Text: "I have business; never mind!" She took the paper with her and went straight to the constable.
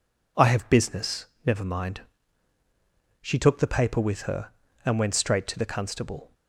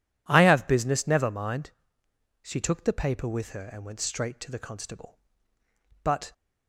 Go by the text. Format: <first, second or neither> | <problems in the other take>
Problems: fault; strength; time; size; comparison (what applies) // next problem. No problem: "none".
first | goes on to say "But"; slight; from 6.0 s on; 0.30 s long